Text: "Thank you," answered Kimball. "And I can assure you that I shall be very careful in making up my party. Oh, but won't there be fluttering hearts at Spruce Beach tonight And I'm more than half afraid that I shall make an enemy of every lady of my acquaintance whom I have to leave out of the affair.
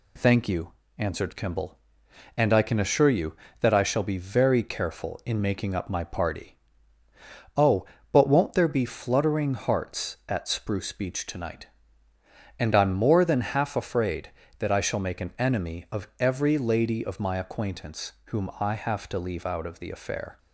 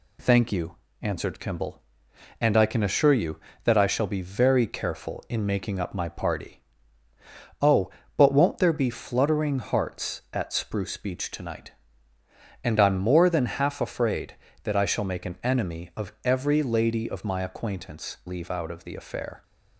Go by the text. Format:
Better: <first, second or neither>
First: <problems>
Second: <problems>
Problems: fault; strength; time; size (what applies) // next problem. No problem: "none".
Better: first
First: none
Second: skips "whom I have to"; at 18.2 s